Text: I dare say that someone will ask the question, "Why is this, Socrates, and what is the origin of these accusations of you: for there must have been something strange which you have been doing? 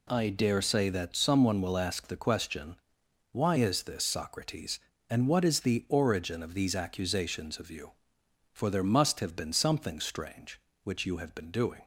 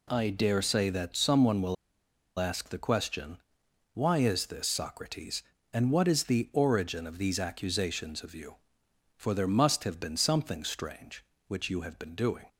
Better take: first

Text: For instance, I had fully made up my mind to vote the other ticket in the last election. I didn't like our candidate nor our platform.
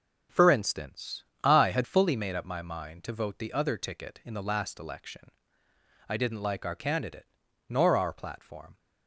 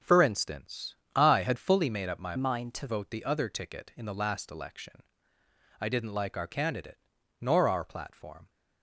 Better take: first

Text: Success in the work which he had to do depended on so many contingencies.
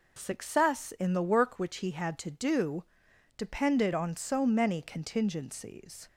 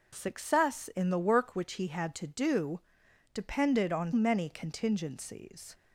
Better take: first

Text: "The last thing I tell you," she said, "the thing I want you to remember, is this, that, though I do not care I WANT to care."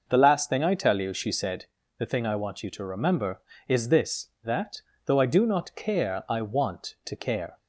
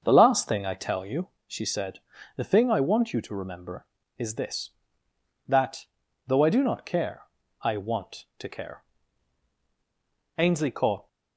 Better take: first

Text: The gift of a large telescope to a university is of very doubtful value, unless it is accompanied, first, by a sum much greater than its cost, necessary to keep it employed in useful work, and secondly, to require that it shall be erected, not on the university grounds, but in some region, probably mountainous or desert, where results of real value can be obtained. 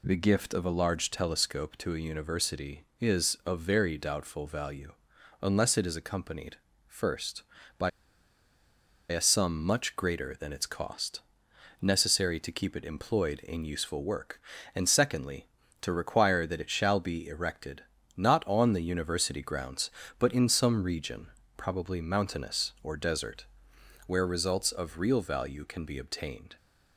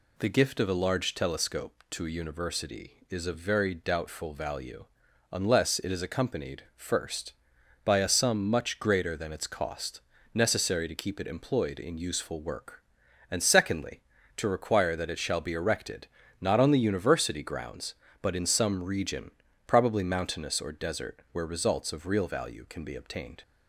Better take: second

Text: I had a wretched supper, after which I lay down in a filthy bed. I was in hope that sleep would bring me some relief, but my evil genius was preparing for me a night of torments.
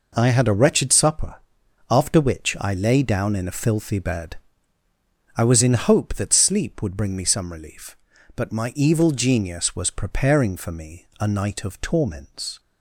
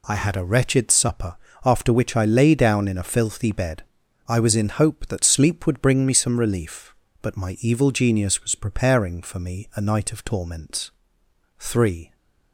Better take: first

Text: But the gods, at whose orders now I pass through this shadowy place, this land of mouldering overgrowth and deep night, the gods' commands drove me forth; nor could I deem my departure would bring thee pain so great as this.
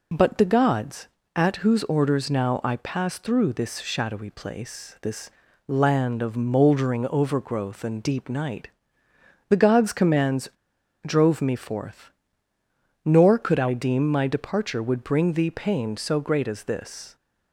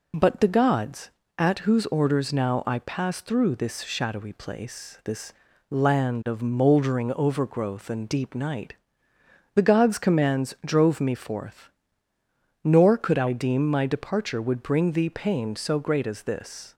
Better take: second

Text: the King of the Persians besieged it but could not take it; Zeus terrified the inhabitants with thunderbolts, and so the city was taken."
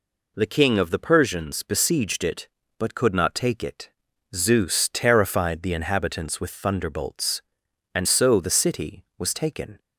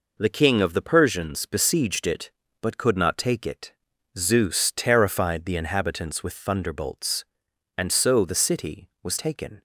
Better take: first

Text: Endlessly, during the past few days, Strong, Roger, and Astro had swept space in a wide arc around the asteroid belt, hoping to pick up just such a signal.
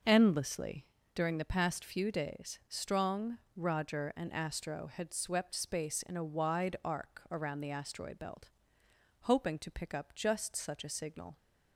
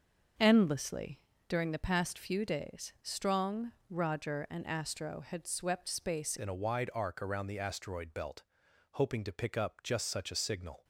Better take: first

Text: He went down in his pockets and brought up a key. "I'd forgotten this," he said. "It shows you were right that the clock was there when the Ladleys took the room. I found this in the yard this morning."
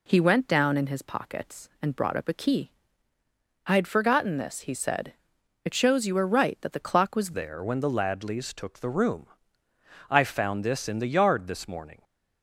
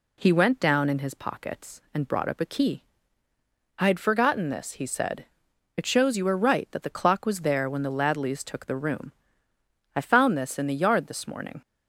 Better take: second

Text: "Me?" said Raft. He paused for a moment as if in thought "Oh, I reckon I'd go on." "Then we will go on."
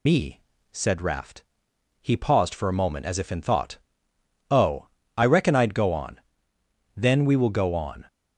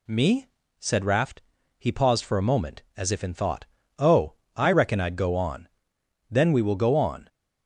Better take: second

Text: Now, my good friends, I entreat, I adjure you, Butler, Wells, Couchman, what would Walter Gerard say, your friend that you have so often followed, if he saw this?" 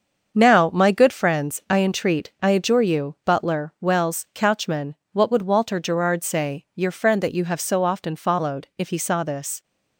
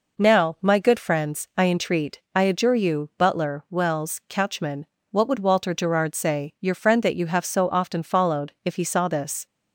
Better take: second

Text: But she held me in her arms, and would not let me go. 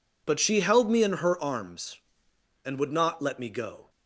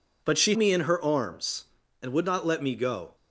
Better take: first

